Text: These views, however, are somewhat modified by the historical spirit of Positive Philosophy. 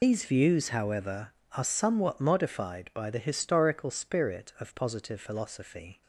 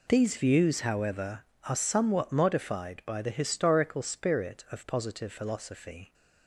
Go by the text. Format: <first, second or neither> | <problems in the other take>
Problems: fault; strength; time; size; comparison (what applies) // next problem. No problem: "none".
second | loses the start of "These"; at 0.0 s; 45 ms